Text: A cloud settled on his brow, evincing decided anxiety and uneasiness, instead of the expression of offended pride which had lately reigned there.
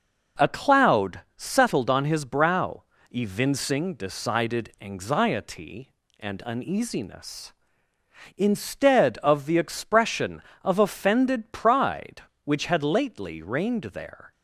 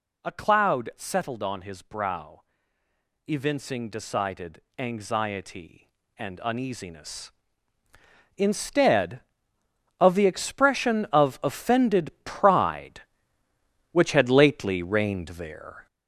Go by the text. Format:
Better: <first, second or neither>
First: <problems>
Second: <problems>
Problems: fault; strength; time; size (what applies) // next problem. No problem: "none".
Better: first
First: none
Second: gets louder; throughout; 6.5 dB // pauses between "decided" and "anxiety"; slight; at 4.6 s; 0.16 s long